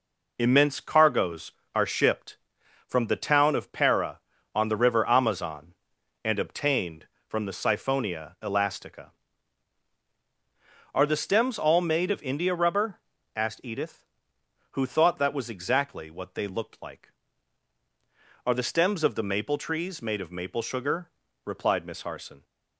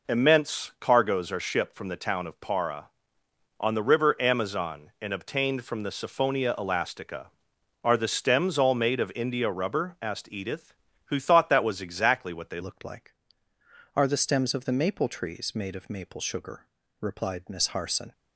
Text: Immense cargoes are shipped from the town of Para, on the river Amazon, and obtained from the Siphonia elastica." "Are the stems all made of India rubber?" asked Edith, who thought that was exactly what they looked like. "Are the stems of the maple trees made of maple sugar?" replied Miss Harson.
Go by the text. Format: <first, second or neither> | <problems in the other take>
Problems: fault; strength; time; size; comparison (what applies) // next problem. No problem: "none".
first | changes voice at "looked"; from 12.6 s on; 5.5 s long